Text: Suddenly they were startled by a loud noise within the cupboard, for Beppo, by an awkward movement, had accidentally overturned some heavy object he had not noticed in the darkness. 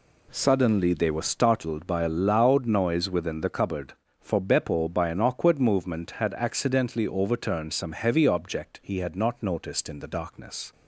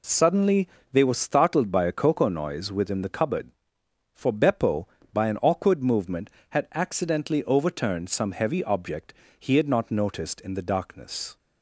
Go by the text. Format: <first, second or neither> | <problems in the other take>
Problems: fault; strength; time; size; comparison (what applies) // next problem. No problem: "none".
first | pauses between "Suddenly" and "they"; slight; at 0.6 s; 0.24 s long // says "cocoa" for "loud"; at 1.9 s // pauses between "object" and "he"; slight; at 9.1 s; 0.24 s long